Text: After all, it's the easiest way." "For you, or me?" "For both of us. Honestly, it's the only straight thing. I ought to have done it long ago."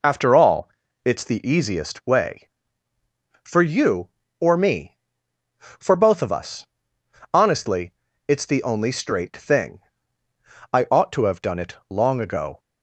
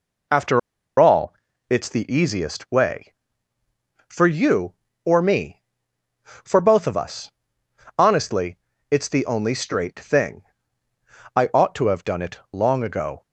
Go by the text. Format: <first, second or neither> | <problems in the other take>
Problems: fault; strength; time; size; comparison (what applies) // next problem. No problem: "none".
first | pauses between "After" and "all"; at 0.5 s; 0.39 s long